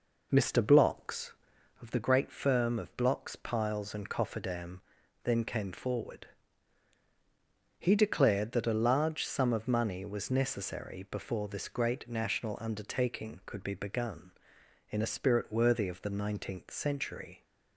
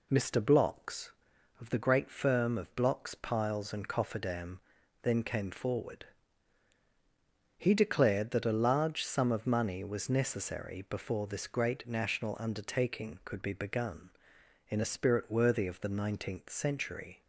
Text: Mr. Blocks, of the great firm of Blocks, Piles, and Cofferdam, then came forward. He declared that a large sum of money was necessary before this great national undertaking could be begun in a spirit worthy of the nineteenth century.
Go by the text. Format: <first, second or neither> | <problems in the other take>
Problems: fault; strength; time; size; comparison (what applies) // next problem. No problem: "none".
second | starts louder than the rest; noticeable; until 1.9 s; 4.5 dB